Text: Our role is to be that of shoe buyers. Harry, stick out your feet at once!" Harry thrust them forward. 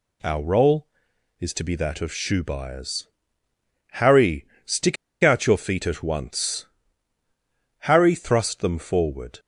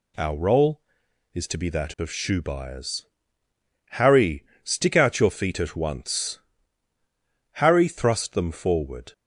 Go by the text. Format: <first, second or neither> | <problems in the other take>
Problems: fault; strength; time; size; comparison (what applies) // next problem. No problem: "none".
second | pauses between "stick" and "out"; slight; at 4.9 s; 0.27 s long